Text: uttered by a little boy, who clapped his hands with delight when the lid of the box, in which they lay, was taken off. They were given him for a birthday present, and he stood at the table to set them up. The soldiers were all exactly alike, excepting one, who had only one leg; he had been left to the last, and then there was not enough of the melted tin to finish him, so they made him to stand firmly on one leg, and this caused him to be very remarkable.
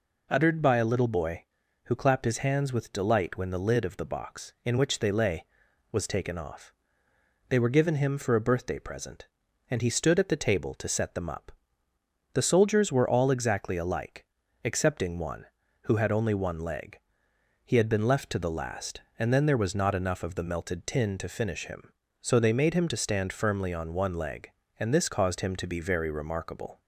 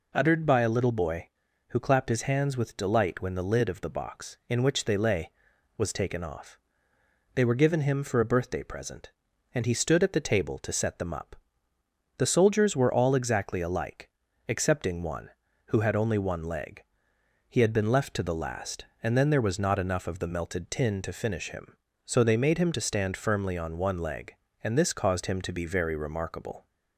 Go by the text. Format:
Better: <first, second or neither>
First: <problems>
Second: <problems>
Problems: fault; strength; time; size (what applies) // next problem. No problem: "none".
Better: neither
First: none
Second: none